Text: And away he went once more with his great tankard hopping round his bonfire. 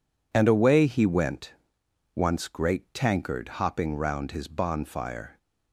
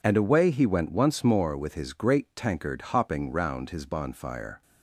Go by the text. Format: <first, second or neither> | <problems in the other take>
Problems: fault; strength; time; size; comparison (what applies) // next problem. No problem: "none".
second | pauses between "went" and "once"; noticeable; at 1.5 s; 0.64 s long // skips "more with his"; at 2.4 s